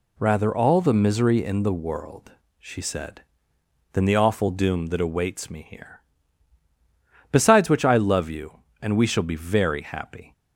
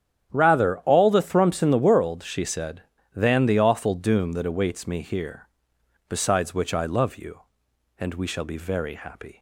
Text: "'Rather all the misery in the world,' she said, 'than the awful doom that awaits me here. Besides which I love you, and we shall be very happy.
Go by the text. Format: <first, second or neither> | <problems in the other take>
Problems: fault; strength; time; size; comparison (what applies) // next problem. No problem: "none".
first | starts louder than the rest; strong; until 1.3 s; 9 dB // says "thrumps" for "misery"; at 1.2 s